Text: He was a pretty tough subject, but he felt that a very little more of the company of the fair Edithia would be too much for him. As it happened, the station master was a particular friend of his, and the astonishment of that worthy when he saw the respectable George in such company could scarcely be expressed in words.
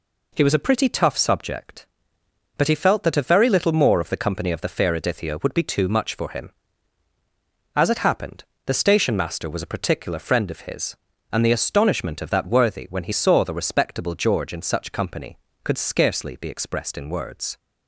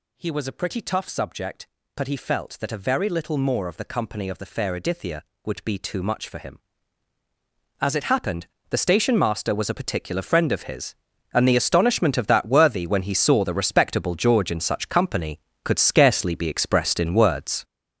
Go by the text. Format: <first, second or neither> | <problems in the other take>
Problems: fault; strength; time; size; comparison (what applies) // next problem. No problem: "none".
first | gets louder; strong; throughout; 8.5 dB